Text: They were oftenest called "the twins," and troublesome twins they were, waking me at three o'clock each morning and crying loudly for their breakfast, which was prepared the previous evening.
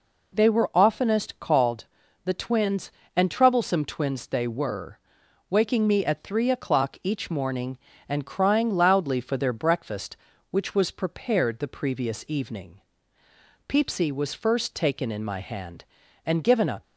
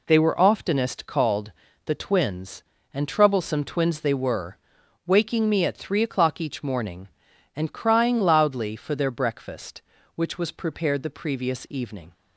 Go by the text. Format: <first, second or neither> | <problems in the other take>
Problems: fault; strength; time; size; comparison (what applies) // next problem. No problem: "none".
second | pauses between "called" and "the"; at 1.8 s; 0.38 s long; slight in the second // goes on to say "Peepsy was first taken in my hand and given a"; strong; from 13.6 s on; 3.1 s long